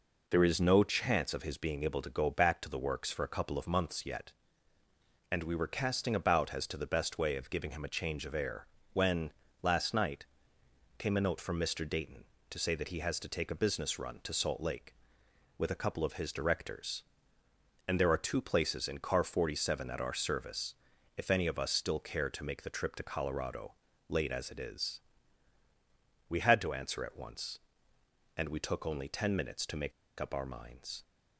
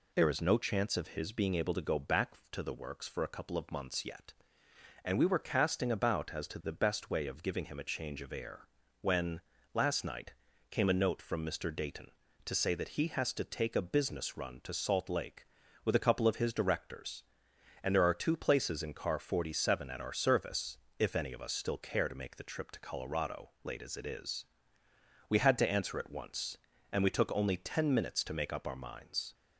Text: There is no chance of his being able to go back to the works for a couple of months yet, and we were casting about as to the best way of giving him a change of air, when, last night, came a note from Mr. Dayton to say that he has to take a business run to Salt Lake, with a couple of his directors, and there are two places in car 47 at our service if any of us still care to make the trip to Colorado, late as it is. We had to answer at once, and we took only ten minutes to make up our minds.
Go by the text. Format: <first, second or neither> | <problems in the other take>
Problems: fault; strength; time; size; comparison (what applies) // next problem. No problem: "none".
second | pauses between "service" and "if"; at 20.7 s; 0.42 s long; slight in the second // pauses between "make" and "up"; slight; at 29.9 s; 0.28 s long